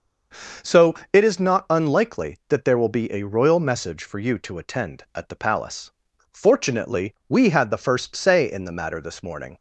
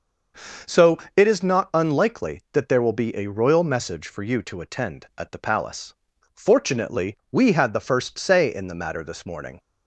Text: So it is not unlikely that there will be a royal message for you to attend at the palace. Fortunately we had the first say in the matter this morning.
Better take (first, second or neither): neither